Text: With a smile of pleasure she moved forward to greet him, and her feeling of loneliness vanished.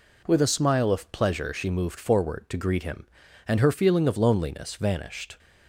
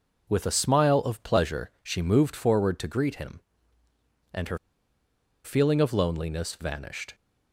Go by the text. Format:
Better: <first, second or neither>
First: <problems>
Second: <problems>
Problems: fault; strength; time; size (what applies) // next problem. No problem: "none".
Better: first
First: none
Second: pauses between "her" and "feeling"; noticeable; at 4.5 s; 0.86 s long